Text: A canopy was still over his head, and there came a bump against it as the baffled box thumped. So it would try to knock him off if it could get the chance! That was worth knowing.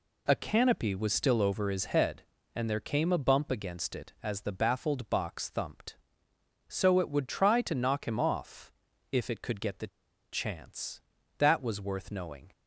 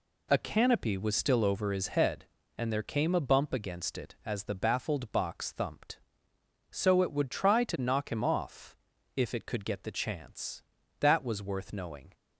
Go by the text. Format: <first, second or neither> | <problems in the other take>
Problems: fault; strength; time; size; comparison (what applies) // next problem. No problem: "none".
second | pauses between "off" and "if"; at 8.7 s; 0.40 s long; also in the second // pauses between "the" and "chance"; at 9.8 s; 0.45 s long